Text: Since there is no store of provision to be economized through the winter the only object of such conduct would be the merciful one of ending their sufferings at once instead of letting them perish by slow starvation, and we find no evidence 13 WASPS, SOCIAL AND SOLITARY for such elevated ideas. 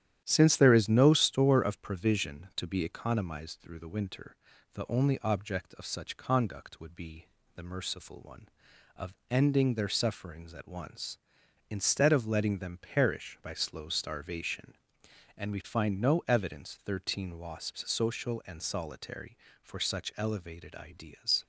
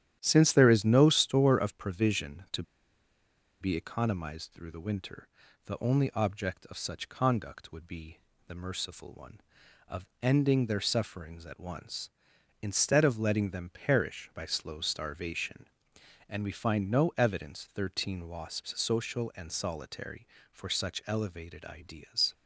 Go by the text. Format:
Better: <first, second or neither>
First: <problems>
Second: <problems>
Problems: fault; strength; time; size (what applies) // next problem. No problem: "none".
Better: first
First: starts louder than the rest; strong; until 1.2 s; 11 dB // pauses between "winter" and "the"; at 4.3 s; 0.38 s long // pauses between "be" and "the"; slight; at 7.2 s; 0.30 s long // pauses between "of" and "ending"; slight; at 9.1 s; 0.16 s long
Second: starts louder than the rest; strong; until 1.2 s; 11 dB // pauses between "to" and "be"; noticeable; at 2.6 s; 0.97 s long // pauses between "winter" and "the"; at 5.2 s; 0.38 s long // pauses between "be" and "the"; slight; at 8.1 s; 0.30 s long // pauses between "of" and "ending"; slight; at 10.0 s; 0.16 s long